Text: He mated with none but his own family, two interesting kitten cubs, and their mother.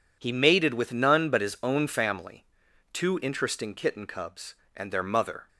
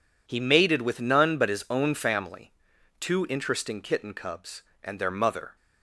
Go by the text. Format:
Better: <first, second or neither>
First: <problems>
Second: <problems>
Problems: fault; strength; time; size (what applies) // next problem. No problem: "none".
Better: neither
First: none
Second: none